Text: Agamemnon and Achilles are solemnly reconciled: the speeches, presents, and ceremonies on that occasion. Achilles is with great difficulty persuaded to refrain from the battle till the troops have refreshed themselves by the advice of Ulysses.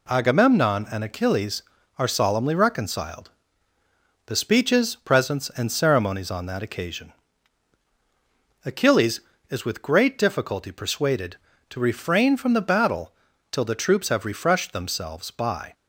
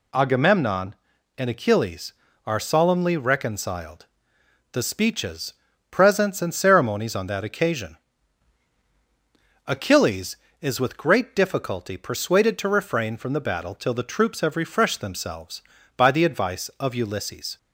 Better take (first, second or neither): second